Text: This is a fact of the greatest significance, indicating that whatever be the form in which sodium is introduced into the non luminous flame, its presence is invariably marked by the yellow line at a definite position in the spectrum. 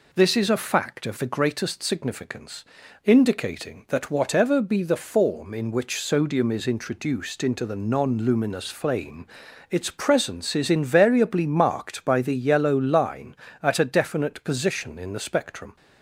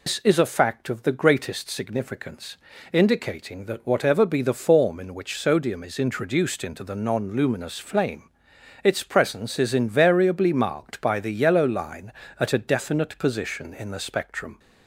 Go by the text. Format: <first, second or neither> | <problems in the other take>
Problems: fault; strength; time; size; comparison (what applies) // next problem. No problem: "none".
first | loses the start of "This"; at 0.0 s; 95 ms